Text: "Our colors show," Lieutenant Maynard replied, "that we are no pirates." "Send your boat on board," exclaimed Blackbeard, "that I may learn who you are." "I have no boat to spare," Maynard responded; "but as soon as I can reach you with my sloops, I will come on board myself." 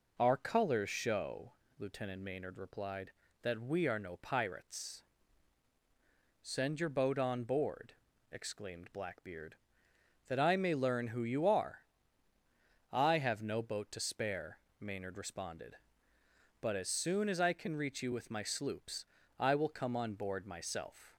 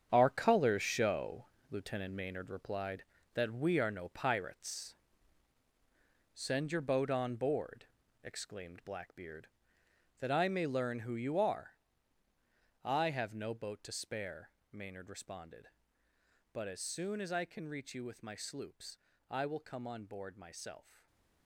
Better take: first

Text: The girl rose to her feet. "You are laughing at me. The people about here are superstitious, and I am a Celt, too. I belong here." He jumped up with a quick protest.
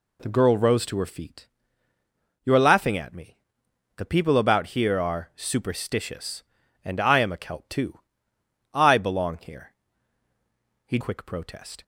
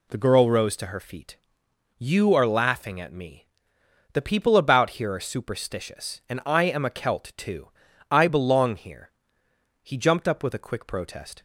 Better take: second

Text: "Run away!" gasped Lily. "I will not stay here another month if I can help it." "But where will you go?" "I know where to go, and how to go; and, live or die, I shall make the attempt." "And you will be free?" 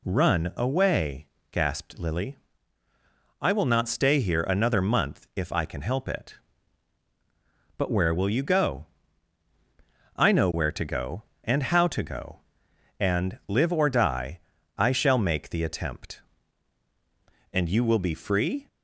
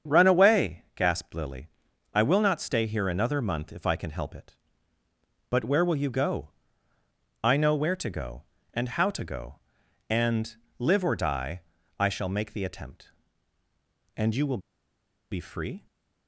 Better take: first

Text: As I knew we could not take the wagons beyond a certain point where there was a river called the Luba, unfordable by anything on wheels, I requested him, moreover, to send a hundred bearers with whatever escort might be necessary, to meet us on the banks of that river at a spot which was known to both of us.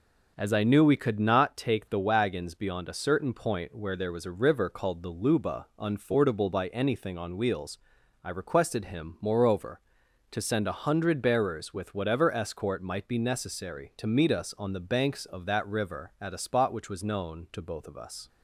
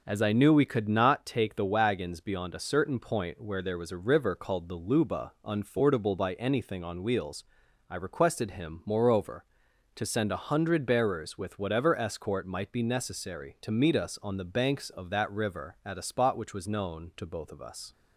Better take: neither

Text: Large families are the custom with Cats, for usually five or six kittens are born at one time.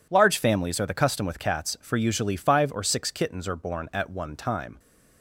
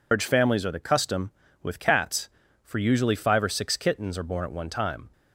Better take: first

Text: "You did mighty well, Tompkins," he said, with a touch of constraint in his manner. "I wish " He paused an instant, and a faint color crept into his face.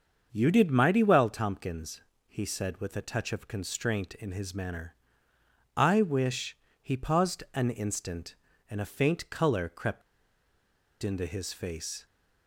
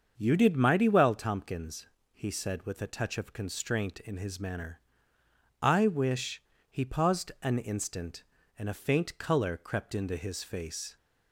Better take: second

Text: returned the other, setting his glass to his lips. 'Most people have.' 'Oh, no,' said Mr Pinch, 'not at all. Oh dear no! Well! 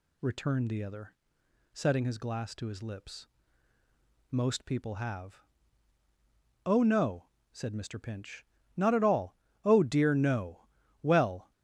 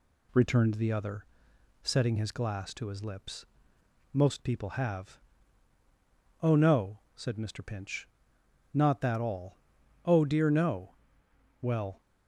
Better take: first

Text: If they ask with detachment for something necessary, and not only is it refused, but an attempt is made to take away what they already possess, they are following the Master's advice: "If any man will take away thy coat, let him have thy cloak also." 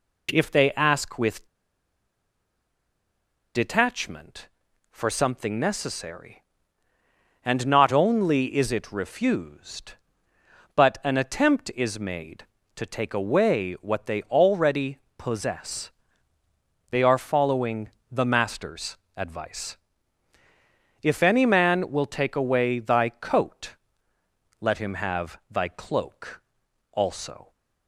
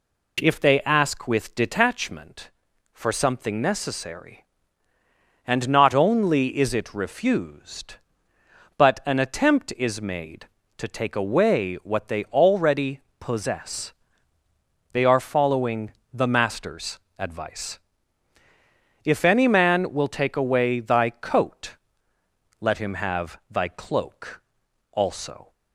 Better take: second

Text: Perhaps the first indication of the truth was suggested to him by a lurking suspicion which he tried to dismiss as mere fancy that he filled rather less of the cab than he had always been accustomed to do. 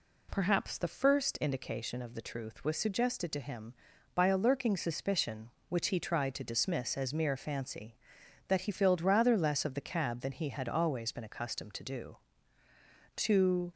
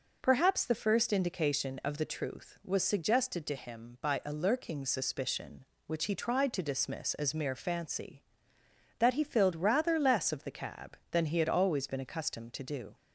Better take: second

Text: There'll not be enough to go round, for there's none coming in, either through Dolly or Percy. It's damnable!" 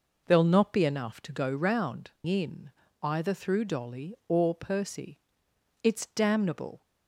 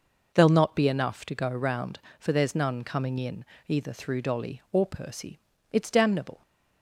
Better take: second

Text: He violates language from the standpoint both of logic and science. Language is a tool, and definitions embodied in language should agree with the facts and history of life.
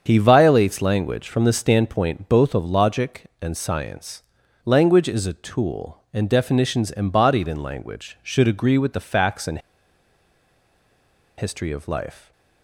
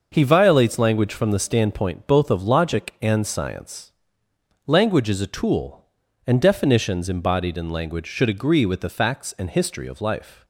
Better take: second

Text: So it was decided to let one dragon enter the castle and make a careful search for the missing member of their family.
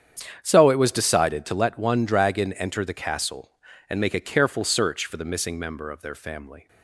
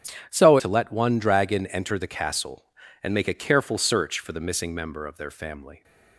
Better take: first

